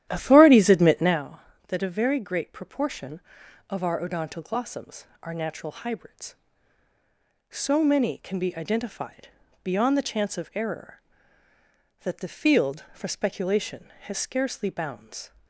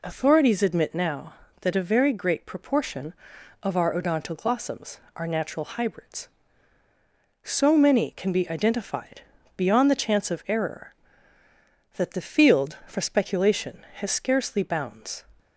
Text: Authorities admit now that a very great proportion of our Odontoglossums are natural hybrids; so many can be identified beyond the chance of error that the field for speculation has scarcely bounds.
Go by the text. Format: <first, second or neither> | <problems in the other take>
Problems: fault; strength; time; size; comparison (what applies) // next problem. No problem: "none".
second | starts louder than the rest; strong; until 1.2 s; 12 dB // pauses between "identified" and "beyond"; slight; at 9.2 s; 0.34 s long; slight in the second